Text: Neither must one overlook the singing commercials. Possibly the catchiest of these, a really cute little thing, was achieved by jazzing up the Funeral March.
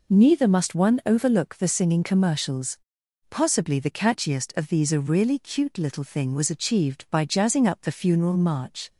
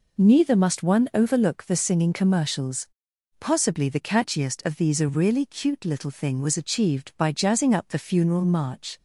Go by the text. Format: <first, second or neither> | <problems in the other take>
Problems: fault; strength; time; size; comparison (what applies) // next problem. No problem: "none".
neither | none